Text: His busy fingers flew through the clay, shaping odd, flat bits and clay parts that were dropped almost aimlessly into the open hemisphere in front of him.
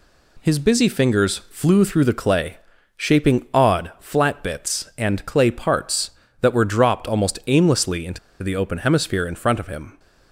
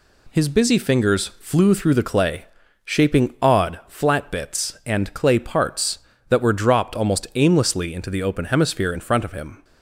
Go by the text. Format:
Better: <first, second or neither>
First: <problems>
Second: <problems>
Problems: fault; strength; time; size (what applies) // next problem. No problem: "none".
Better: second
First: pauses between "into" and "the"; slight; at 8.1 s; 0.24 s long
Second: none